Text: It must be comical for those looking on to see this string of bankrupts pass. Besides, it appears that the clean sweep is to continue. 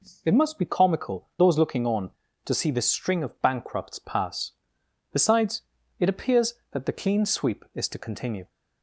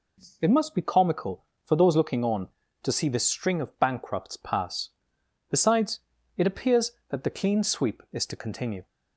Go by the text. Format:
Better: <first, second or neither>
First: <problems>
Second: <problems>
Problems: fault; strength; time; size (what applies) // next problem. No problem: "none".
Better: second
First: skips "for"; at 1.3 s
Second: none